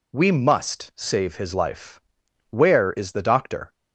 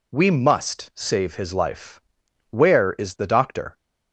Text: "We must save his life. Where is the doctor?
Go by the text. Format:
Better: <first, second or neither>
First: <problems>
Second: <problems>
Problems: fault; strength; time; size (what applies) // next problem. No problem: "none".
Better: neither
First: none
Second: none